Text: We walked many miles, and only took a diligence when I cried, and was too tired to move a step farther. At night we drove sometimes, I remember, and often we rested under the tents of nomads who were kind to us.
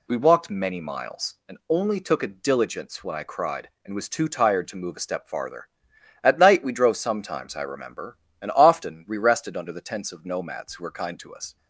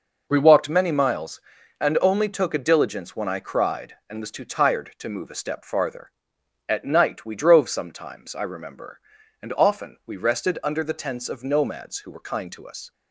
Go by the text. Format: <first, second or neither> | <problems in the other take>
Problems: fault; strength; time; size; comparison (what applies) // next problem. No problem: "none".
neither | none